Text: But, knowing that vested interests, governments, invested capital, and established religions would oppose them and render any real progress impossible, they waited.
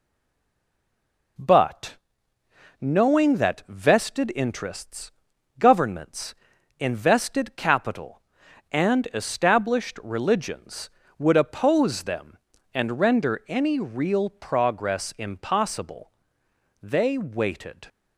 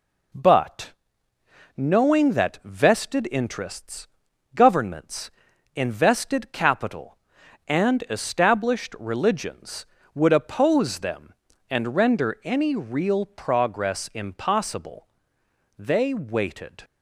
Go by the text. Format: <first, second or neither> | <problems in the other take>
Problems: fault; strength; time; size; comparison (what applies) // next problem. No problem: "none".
second | stays silent before the first word; noticeable; until 1.3 s; 1.3 s long